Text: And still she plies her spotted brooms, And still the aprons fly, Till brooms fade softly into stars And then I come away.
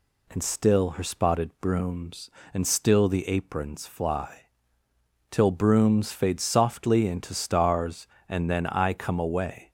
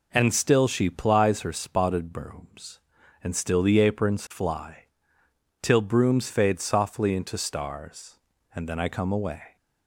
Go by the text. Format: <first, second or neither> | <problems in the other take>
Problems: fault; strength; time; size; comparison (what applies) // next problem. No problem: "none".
second | skips "she plies"; at 0.9 s